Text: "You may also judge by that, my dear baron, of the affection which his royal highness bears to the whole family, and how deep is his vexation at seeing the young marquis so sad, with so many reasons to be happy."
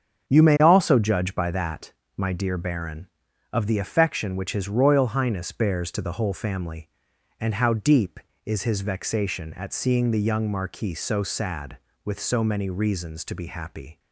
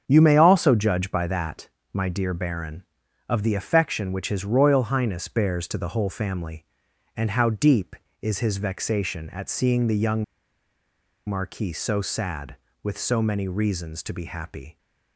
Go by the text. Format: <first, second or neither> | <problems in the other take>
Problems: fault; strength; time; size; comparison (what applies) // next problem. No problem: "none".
first | starts louder than the rest; strong; until 1.0 s; 8 dB; strong in the first // pauses between "young" and "marquis"; at 10.2 s; 1.0 s long